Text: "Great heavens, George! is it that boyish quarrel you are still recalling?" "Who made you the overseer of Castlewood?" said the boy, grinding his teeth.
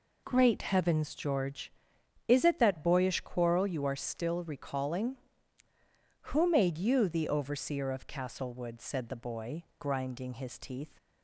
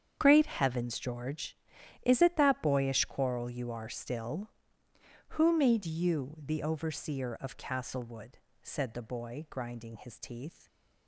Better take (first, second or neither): first